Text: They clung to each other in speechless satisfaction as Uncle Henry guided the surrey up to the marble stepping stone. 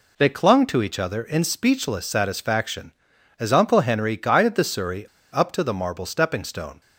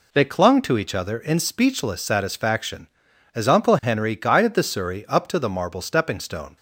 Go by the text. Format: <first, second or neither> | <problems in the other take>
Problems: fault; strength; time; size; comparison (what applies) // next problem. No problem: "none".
second | pauses between "surrey" and "up"; slight; at 5.0 s; 0.27 s long